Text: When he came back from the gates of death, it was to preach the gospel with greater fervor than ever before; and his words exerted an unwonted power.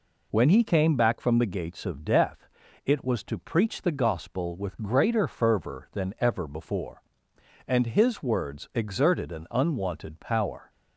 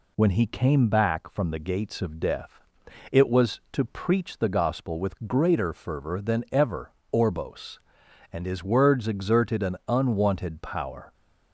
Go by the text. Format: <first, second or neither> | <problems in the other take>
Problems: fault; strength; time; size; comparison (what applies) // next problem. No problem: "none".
first | says "orbos" for "before"; at 7.1 s